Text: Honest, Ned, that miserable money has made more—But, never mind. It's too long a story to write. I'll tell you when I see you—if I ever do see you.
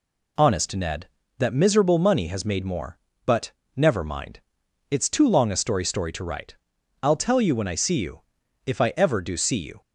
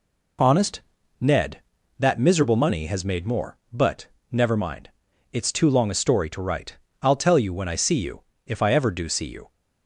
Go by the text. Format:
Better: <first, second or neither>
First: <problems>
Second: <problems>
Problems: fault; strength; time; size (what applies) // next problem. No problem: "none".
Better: second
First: says "story" twice; at 5.8 s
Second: none